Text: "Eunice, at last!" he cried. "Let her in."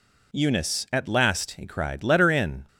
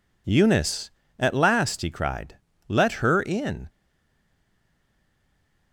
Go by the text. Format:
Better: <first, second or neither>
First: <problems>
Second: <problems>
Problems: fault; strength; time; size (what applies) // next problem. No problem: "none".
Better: first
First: none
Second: stays silent after the last word; noticeable; from 3.6 s on; 2.1 s long